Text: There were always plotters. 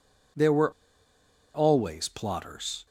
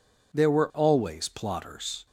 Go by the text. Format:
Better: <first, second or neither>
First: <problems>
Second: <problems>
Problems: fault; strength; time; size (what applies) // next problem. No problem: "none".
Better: second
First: pauses between "were" and "always"; noticeable; at 0.7 s; 0.82 s long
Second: none